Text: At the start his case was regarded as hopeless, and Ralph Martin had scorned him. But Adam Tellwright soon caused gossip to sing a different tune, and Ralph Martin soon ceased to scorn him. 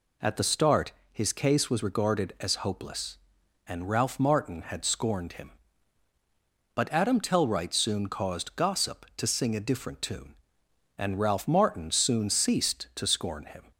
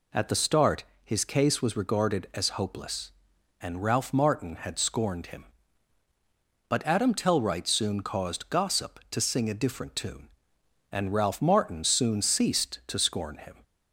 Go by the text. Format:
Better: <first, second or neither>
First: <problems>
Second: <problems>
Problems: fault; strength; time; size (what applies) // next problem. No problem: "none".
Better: neither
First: pauses between "start" and "his"; slight; at 0.9 s; 0.20 s long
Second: pauses between "start" and "his"; slight; at 0.8 s; 0.20 s long